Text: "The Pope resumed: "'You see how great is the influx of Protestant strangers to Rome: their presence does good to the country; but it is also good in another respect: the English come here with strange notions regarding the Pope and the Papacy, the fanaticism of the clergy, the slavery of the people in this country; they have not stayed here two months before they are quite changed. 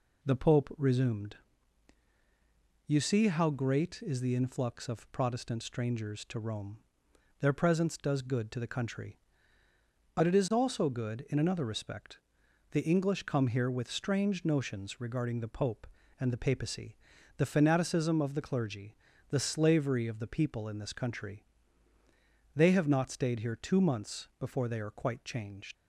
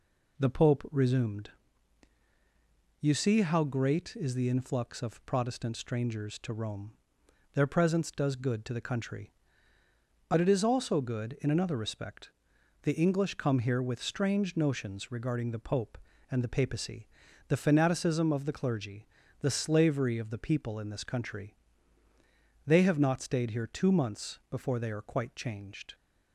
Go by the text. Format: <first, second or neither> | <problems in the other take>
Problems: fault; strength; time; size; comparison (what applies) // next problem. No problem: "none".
second | leaves "changed" unfinished; at 25.7 s; 85 ms